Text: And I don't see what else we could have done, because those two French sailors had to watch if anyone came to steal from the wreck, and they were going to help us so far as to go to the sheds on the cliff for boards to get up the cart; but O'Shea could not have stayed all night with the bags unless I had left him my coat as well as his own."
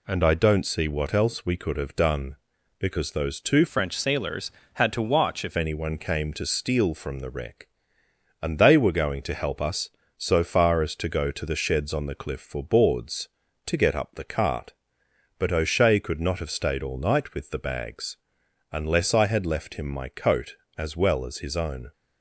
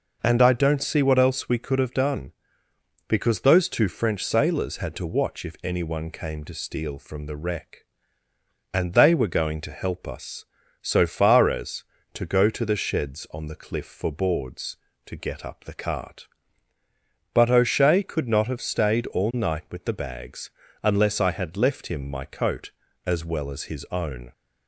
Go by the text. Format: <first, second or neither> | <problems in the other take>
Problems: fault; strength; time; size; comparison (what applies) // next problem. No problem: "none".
second | changes voice from "French" to "if"; from 3.6 to 5.5 s; 1.9 s long // pauses between "bags" and "unless"; noticeable; at 18.1 s; 0.54 s long; slight in the second